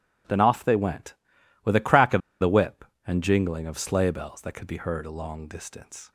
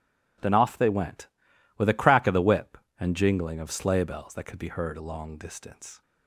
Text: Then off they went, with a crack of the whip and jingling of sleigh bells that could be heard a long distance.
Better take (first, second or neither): second